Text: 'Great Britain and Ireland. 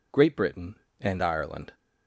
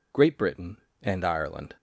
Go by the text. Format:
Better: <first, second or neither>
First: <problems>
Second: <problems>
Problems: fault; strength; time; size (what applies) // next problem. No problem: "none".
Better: neither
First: none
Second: none